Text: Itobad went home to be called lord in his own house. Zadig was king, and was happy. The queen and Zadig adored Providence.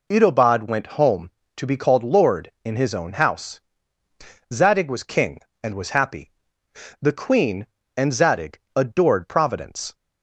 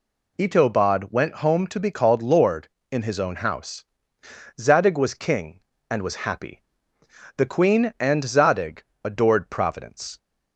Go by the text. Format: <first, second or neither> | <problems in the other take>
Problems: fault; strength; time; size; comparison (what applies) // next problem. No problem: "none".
neither | pauses between "Zadig" and "adored"; slight; the same in both